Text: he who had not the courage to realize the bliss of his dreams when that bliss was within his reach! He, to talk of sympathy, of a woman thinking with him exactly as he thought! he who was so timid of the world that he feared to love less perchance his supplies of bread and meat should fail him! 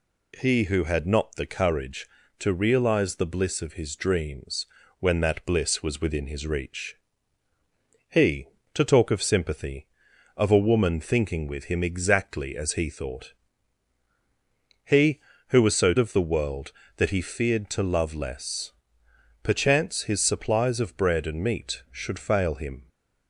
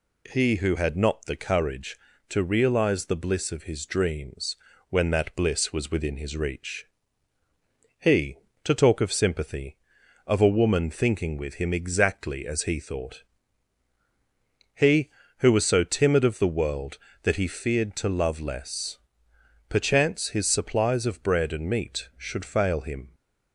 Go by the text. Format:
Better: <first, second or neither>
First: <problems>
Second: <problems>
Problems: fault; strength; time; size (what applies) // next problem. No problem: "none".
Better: second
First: pauses between "dreams" and "when"; slight; at 4.6 s; 0.32 s long // skips "timid"; at 15.9 s // pauses between "less" and "perchance"; noticeable; at 18.7 s; 0.70 s long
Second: pauses between "dreams" and "when"; slight; at 4.5 s; 0.32 s long // pauses between "less" and "perchance"; noticeable; at 18.9 s; 0.70 s long